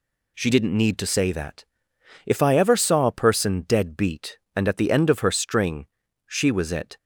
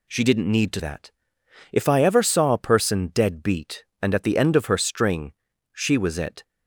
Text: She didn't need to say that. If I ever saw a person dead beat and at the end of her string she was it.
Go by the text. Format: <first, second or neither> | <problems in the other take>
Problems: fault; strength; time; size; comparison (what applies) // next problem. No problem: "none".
first | skips "say"; at 0.7 s // pauses between "string" and "she"; at 5.3 s; 0.40 s long; also in the first